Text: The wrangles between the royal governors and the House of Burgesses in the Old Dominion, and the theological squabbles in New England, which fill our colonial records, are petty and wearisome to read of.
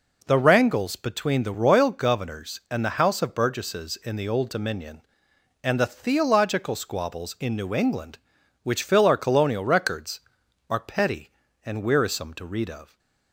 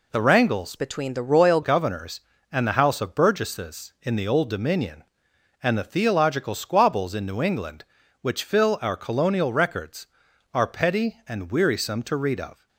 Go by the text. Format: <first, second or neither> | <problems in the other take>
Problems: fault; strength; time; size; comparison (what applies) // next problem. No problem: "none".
first | changes voice from "between" to "royal"; from 0.7 to 1.6 s; 0.9 s long